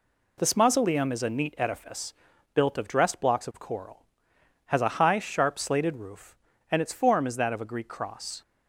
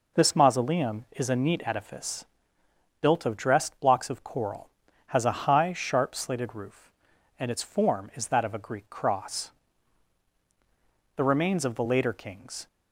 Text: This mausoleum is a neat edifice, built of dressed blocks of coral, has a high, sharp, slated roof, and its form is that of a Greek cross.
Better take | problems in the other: first | goes on to say "The remains of the later Kings"; from 11.1 s on; 1.5 s long

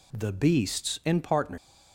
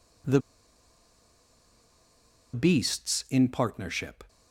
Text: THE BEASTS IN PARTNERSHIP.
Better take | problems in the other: first | pauses between "THE" and "BEASTS"; strong; at 0.3 s; 2.1 s long

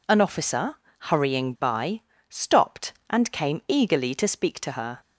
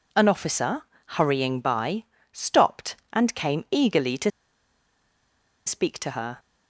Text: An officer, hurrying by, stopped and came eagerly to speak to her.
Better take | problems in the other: first | pauses between "to" and "speak"; strong; at 4.3 s; 1.3 s long

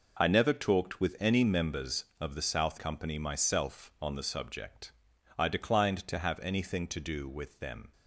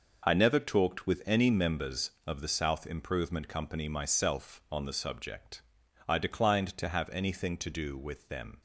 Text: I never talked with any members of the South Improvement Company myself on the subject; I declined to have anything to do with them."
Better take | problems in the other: second | skips "Improvement"; at 2.7 s

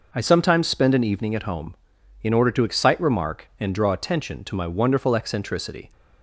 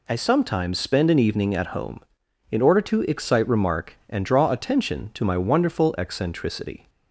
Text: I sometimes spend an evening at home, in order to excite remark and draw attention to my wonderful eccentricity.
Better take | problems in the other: neither | none

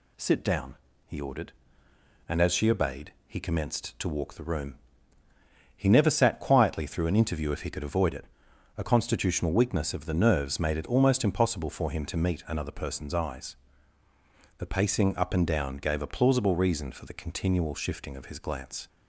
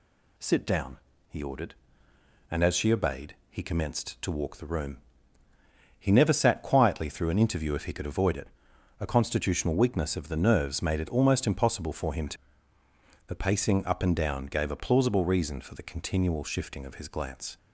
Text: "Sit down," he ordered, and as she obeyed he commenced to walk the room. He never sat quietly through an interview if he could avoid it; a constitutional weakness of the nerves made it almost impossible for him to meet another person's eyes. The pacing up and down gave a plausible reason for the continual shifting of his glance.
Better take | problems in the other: first | skips "meet another person's eyes"; at 12.8 s

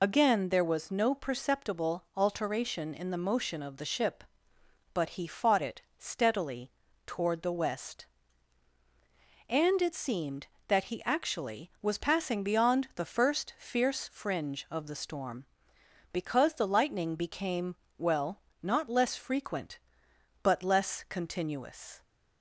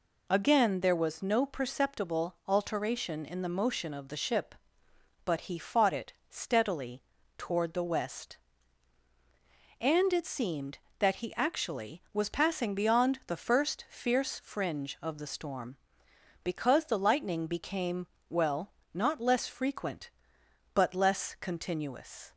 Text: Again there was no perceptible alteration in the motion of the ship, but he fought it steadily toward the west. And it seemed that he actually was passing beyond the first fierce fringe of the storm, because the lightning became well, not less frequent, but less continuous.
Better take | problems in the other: second | loses the start of "Again"; at 0.0 s; 35 ms // pauses between "it" and "steadily"; slight; at 5.8 s; 0.16 s long; slight in the second // pauses between "steadily" and "toward"; slight; at 6.7 s; 0.34 s long; slight in the second // pauses between "became" and "well"; slight; at 17.7 s; 0.20 s long; slight in the second

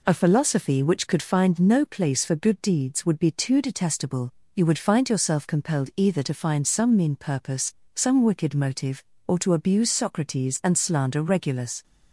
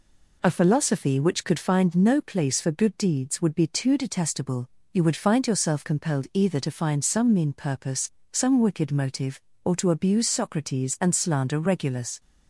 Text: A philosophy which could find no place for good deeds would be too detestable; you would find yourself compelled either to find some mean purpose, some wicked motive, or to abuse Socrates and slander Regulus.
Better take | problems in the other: neither | none

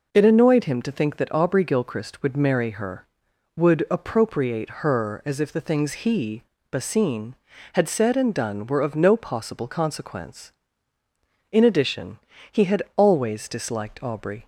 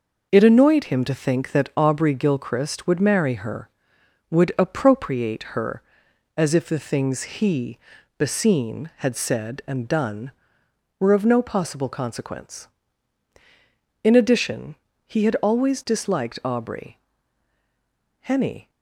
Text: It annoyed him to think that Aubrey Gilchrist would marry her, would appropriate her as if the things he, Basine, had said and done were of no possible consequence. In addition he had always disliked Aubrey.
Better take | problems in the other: first | pauses between "addition" and "he"; slight; at 14.7 s; 0.32 s long; slight in the first // goes on to say "Henny"; slight; from 18.2 s on; 0.48 s long

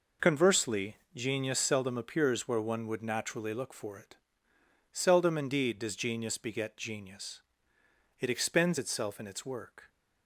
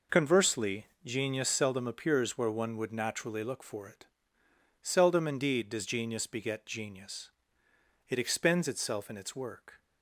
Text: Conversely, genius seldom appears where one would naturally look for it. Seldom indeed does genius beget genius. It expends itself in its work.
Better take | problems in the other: neither | none

